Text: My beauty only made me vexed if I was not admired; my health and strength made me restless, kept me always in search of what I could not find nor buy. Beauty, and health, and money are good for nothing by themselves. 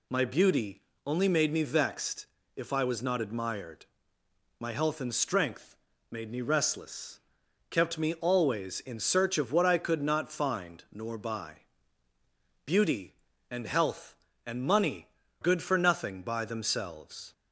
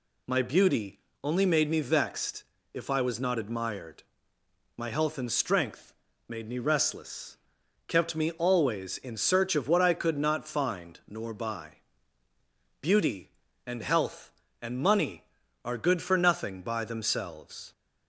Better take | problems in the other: second | pauses between "beauty" and "only"; slight; at 0.8 s; 0.24 s long; slight in the second // pauses between "vexed" and "if"; slight; at 2.2 s; 0.30 s long; slight in the second // pauses between "strength" and "made"; slight; at 5.7 s; 0.34 s long; slight in the second // skips "are"; at 15.2 s

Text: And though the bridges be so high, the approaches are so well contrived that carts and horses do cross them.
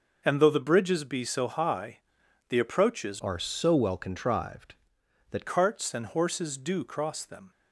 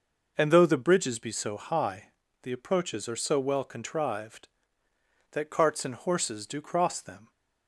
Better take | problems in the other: second | changes voice from "are" to "that"; from 3.2 to 5.4 s; 2.2 s long

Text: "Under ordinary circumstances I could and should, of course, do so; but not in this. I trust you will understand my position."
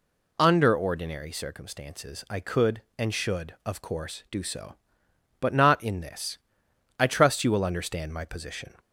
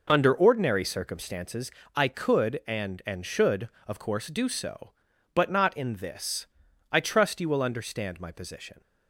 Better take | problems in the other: first | pauses between "circumstances" and "I"; slight; at 1.7 s; 0.24 s long // says "and" twice; at 3.0 s

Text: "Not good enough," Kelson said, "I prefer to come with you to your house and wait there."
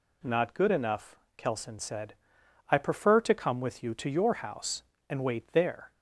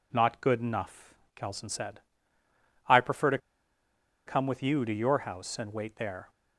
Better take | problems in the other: first | pauses between "to" and "come"; noticeable; at 3.3 s; 0.89 s long

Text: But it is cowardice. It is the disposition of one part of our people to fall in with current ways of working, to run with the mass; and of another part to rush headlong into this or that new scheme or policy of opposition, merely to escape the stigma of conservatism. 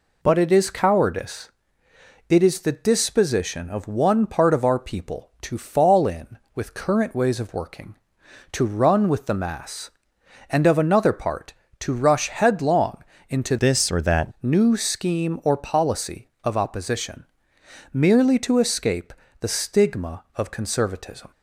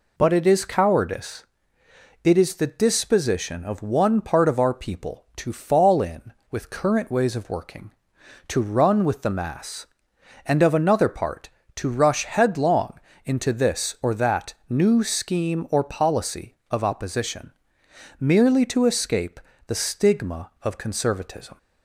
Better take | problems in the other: second | pauses between "headlong" and "into"; slight; at 13.0 s; 0.28 s long; slight in the second // changes voice from "this" to "that"; from 13.5 to 14.3 s; 0.8 s long // pauses between "escape" and "the"; slight; at 19.1 s; 0.28 s long; slight in the second

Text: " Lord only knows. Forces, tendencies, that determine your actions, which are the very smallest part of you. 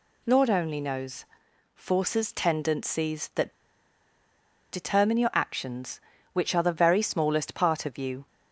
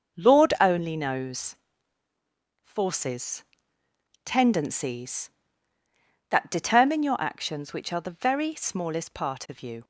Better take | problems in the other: second | pauses between "that" and "determine"; at 3.5 s; 1.2 s long

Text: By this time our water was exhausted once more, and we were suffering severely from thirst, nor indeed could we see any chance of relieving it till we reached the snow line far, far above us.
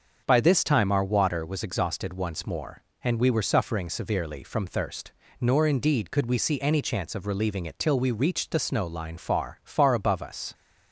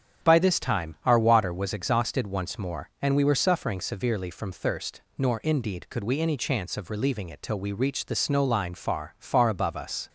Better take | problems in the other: first | starts louder than the rest; strong; until 1.3 s; 9 dB; also in the first // skips "see"; at 6.2 s

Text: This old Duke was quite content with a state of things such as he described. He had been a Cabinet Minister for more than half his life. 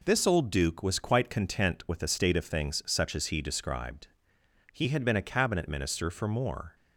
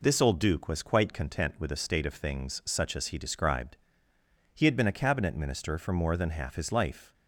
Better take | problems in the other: second | stops before "than half his life"; at 6.7 s

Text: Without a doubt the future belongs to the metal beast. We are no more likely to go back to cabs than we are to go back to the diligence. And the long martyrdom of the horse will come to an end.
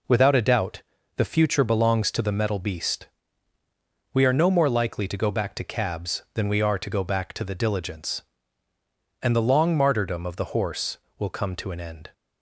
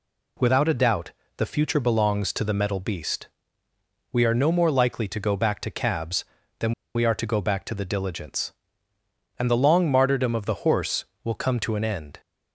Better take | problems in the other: first | pauses between "doubt" and "the"; slight; at 1.1 s; 0.26 s long; slight in the first // pauses between "than" and "we"; slight; at 6.7 s; 0.23 s long

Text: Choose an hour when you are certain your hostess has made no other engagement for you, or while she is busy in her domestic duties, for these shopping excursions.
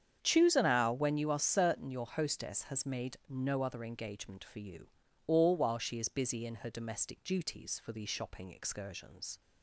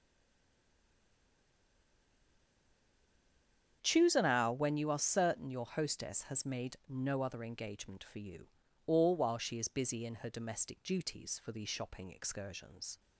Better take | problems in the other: first | stays silent before the first word; strong; until 3.8 s; 3.8 s long // starts louder than the rest; strong; until 4.8 s; 8 dB; strong in the first

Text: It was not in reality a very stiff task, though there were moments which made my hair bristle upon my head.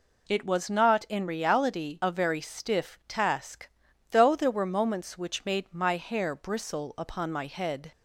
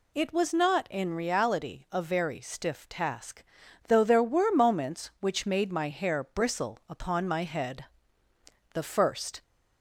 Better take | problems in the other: first | goes on to say "The first"; noticeable; from 8.7 s on; 0.70 s long

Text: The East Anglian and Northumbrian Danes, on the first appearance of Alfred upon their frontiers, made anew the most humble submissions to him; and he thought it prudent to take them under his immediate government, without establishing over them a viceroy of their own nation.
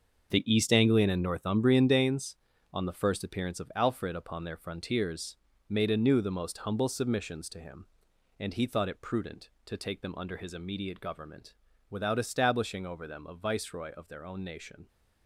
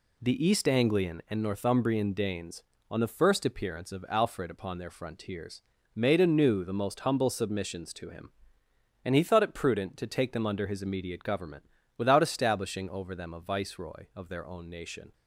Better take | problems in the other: second | gets quieter; strong; throughout; 10.5 dB

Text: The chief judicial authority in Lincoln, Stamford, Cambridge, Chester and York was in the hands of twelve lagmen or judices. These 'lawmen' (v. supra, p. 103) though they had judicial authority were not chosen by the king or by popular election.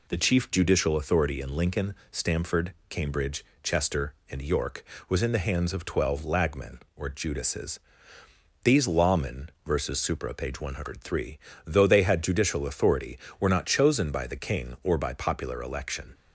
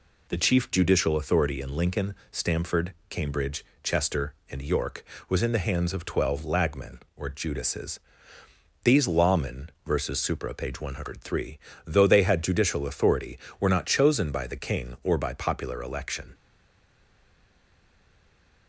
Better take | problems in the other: first | stays silent after the last word; from 16.3 s on; 2.3 s long

